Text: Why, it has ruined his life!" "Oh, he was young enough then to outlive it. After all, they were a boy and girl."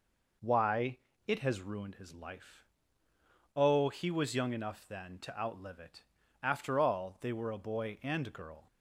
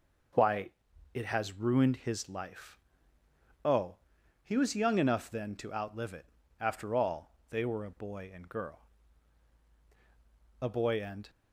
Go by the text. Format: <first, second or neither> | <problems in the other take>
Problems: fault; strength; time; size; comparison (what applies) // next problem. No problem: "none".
first | goes on to say "A boy and"; noticeable; from 10.5 s on; 0.70 s long